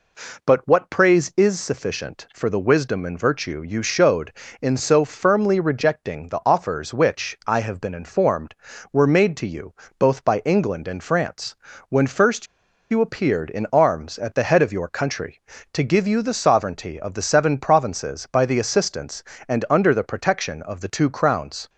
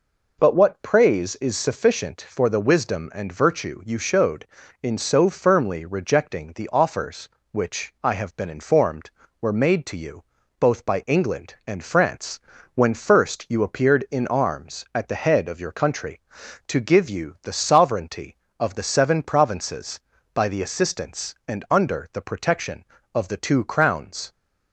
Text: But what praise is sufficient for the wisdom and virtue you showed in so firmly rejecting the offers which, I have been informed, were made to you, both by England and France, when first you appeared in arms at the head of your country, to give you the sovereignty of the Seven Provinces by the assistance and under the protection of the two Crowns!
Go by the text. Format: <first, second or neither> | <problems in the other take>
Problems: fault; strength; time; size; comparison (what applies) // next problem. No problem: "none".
second | pauses between "first" and "you"; at 12.4 s; 0.44 s long